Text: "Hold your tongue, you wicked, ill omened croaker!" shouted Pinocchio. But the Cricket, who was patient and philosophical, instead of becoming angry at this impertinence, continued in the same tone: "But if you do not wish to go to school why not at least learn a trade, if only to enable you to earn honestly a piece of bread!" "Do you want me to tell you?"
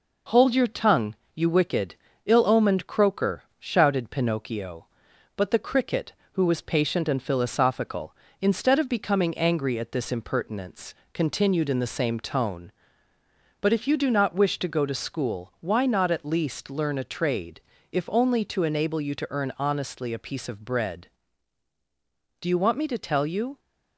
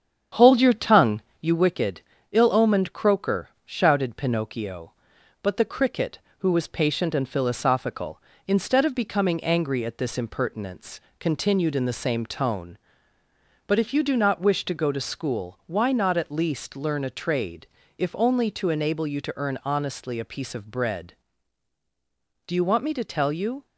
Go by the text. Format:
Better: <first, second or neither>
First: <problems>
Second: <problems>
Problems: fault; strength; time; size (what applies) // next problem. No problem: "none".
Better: first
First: none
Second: starts louder than the rest; strong; until 1.6 s; 8.5 dB